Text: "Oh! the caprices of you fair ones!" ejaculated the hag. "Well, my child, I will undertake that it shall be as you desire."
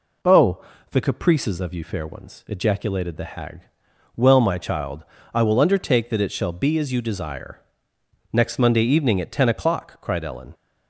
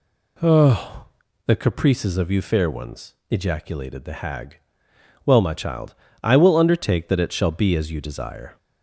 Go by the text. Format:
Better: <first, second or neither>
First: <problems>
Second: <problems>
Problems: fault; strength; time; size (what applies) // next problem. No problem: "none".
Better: second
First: goes on to say "Next Monday evening at ten o'clock cried Ellen"; strong; from 8.3 s on; 2.2 s long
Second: none